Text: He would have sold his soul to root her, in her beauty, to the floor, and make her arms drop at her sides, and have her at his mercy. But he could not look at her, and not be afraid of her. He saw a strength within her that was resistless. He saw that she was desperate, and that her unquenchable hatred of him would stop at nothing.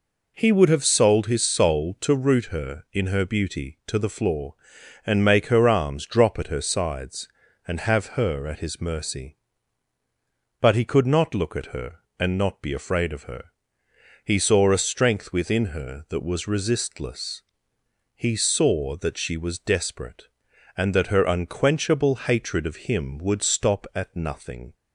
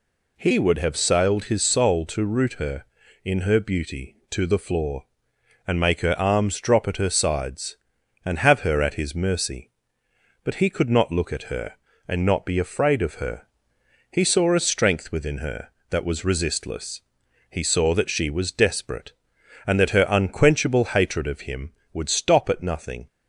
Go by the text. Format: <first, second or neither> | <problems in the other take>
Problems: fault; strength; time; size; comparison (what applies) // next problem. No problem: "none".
first | says "sailed" for "sold"; at 0.9 s